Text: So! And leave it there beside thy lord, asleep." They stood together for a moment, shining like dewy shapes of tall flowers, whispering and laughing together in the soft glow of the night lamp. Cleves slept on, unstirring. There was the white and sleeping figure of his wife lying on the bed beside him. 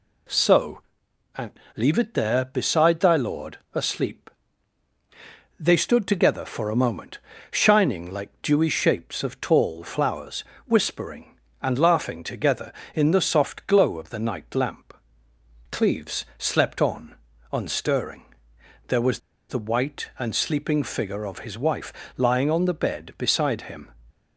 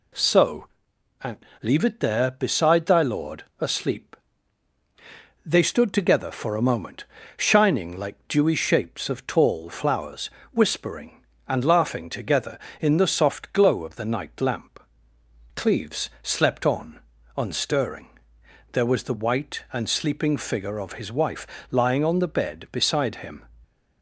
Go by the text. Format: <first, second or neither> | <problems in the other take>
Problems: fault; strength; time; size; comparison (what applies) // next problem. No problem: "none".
second | pauses between "And" and "leave"; slight; at 1.5 s; 0.24 s long; slight in the second // pauses between "was" and "the"; slight; at 19.1 s; 0.29 s long // pauses between "wife" and "lying"; slight; at 21.9 s; 0.24 s long; slight in the second